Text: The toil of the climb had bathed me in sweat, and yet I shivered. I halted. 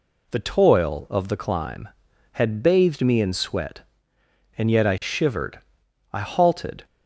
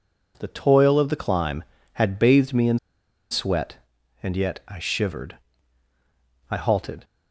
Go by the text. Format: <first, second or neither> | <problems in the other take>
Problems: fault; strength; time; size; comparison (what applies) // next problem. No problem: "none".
first | pauses between "in" and "sweat"; noticeable; at 2.7 s; 0.53 s long